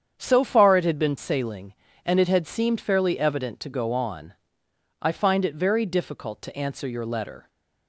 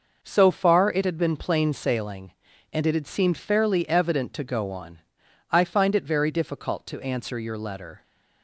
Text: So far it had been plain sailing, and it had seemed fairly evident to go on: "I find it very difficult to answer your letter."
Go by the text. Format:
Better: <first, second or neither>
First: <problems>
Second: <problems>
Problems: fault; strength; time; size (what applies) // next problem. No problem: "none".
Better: second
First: starts louder than the rest; strong; until 1.2 s; 8 dB // skips "plain"; at 1.1 s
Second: none